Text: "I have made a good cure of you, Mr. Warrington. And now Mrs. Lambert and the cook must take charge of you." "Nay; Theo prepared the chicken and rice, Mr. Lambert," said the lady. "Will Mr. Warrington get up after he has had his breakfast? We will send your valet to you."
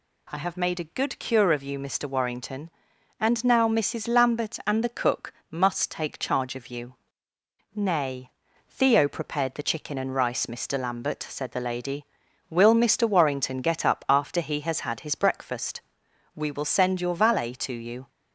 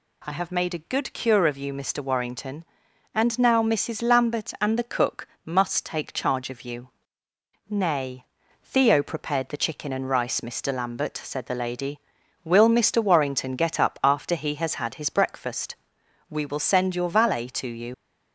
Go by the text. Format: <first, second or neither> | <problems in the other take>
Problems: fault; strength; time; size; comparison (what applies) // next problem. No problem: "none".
first | pauses between "cook" and "must"; slight; at 5.2 s; 0.18 s long; slight in the first // leaves "you" unfinished; at 17.9 s; 80 ms